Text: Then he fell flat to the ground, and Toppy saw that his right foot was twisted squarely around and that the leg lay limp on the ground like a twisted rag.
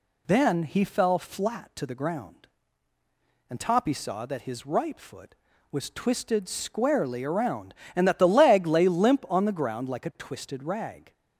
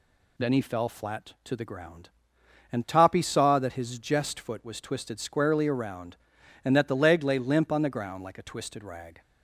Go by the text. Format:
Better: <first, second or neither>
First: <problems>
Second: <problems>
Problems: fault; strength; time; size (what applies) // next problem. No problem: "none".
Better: first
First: none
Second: says "jest" for "right"; at 3.9 s